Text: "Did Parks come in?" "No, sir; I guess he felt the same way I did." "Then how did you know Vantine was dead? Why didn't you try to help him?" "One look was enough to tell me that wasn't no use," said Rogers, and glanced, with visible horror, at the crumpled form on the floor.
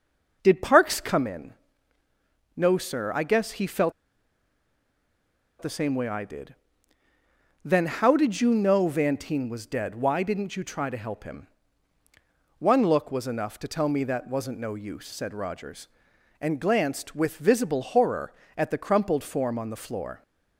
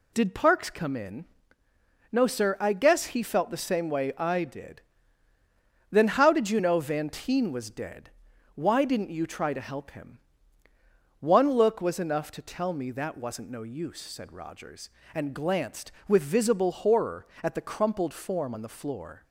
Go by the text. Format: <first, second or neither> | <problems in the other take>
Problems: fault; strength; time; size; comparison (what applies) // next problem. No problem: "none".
second | pauses between "felt" and "the"; strong; at 3.9 s; 1.6 s long